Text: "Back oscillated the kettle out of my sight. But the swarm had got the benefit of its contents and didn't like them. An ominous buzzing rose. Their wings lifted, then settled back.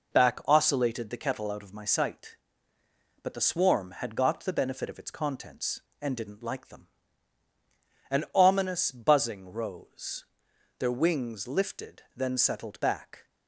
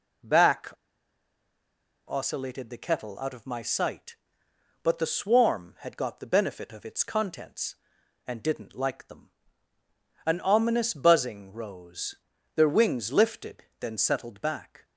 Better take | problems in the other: first | pauses between "Back" and "oscillated"; strong; at 0.7 s; 1.3 s long

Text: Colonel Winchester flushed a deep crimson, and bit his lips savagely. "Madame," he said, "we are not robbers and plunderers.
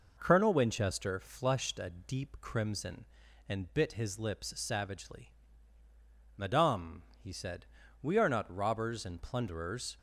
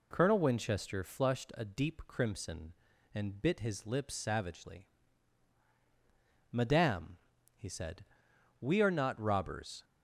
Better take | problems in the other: first | stops before "and plunderers"; at 9.8 s

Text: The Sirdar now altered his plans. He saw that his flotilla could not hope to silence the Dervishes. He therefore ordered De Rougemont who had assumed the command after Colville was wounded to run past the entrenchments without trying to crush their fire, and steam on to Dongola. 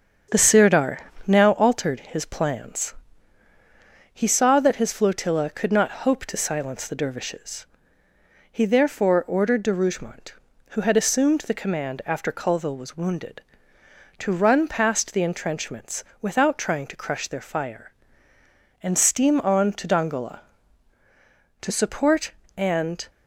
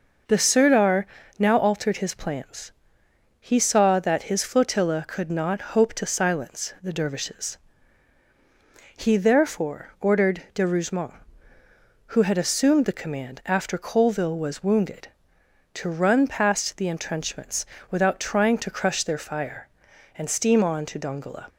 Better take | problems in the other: second | starts louder than the rest; strong; until 1.5 s; 7.5 dB // pauses between "Sirdar" and "now"; slight; at 0.9 s; 0.26 s long; slight in the second // pauses between "entrenchments" and "without"; slight; at 16.0 s; 0.18 s long; slight in the second // goes on to say "To support and"; from 21.6 s on; 1.4 s long

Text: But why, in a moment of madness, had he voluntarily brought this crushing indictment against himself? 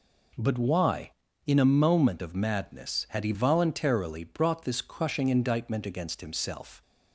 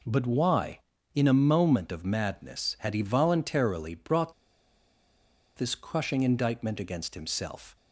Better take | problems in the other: first | pauses between "brought" and "this"; at 4.3 s; 1.2 s long

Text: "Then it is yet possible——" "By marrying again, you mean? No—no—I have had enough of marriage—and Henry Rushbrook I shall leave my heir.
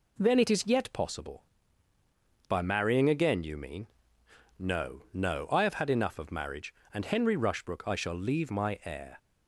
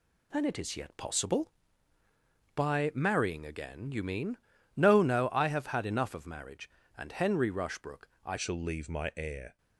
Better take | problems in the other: first | pauses between "Rushbrook" and "I"; slight; at 8.0 s; 0.16 s long // changes voice at "shall"; from 8.3 s on; 1.2 s long

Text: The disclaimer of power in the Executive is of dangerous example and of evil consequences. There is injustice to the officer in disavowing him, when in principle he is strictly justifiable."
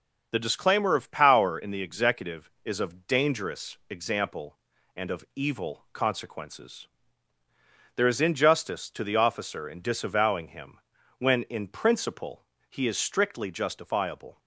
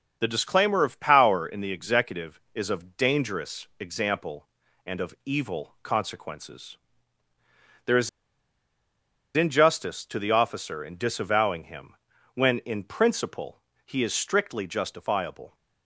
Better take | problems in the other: first | starts louder than the rest; until 1.2 s; 6.5 dB; also in the first // pauses between "is" and "injustice"; strong; at 8.0 s; 1.2 s long // pauses between "principle" and "he"; slight; at 13.5 s; 0.26 s long; slight in the first

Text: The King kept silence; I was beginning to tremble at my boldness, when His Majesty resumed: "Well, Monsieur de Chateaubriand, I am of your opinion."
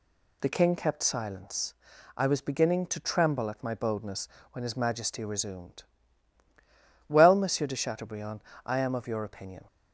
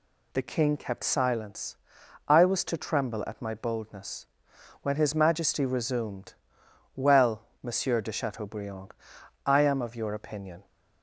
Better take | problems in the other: first | skips "beginning"; at 2.6 s

